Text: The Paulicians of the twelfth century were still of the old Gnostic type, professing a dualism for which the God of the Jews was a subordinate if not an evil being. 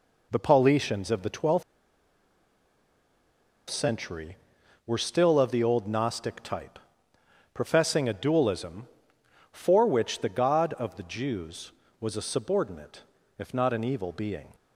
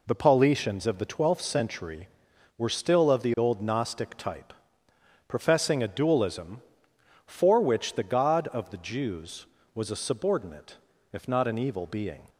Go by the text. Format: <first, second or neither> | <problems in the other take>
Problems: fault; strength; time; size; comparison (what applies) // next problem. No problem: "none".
second | pauses between "twelfth" and "century"; strong; at 1.6 s; 2.0 s long // pauses between "subordinate" and "if"; slight; at 13.0 s; 0.34 s long; slight in the second